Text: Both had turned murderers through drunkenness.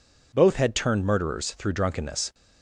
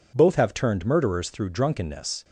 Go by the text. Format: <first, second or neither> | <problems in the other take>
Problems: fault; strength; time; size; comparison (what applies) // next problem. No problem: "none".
first | says "have" for "had"; at 0.3 s